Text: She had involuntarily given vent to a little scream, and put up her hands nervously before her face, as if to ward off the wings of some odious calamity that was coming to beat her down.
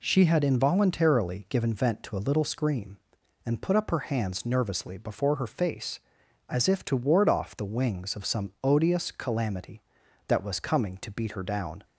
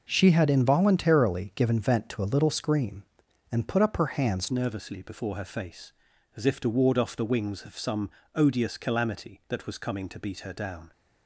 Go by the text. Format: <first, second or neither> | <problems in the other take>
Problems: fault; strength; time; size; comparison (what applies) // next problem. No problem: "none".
first | changes voice at "nervously"; from 4.4 s on; 6.5 s long // pauses between "some" and "odious"; slight; at 8.0 s; 0.26 s long